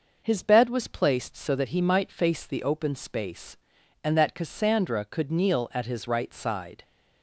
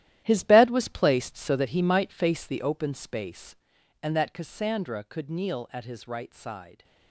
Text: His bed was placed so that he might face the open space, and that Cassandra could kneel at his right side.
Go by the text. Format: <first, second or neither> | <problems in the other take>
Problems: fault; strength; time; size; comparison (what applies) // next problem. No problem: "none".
first | gets quieter; strong; throughout; 12.5 dB